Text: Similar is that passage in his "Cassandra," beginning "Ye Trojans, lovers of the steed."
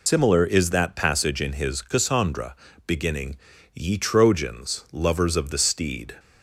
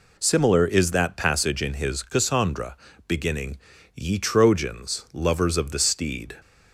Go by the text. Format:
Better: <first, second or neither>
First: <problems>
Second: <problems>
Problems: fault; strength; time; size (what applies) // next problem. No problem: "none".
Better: second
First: loses the start of "Similar"; at 0.0 s; 80 ms // pauses between "beginning" and "Ye"; at 3.3 s; 0.40 s long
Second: pauses between "beginning" and "Ye"; at 3.5 s; 0.40 s long